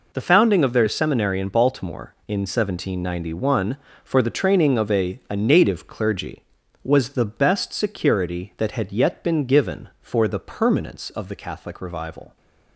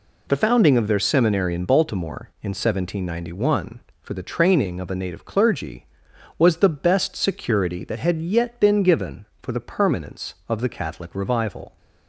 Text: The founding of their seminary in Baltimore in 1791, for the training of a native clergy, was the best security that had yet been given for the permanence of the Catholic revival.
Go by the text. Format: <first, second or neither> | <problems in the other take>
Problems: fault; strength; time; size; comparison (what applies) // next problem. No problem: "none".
second | says "a" twice; at 5.2 s